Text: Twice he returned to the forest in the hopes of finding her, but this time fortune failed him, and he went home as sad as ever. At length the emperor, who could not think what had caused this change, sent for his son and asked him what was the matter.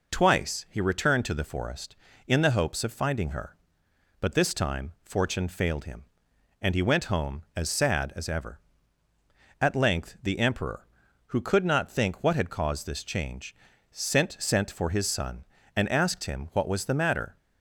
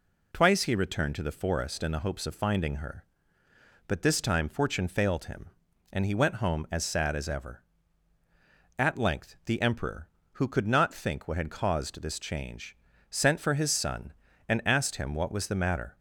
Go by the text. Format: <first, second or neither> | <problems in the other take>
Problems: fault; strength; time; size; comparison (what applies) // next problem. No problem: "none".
second | says "sent" twice; at 14.3 s